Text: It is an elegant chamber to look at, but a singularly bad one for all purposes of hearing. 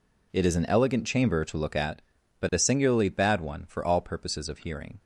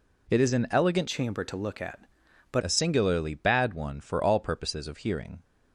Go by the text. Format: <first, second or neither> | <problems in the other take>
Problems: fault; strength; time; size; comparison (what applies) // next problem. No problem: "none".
first | changes voice from "chamber" to "but"; from 1.0 to 2.6 s; 1.6 s long